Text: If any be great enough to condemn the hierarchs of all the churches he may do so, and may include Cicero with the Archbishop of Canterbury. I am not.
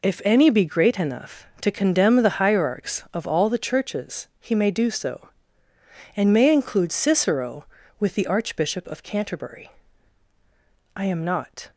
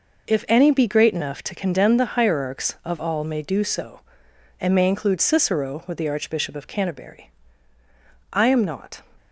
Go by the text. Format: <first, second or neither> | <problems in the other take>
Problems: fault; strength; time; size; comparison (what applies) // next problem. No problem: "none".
first | skips "the churches he"; at 3.2 s